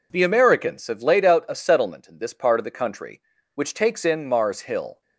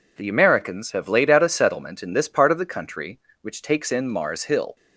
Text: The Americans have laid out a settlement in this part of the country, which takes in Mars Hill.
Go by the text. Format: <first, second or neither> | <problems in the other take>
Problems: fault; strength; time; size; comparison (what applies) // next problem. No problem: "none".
neither | none